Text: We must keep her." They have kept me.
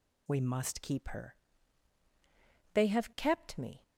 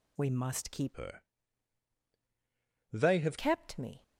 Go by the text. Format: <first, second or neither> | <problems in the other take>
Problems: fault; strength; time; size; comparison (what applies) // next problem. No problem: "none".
first | changes voice from "her" to "have"; from 0.9 to 3.3 s; 2.4 s long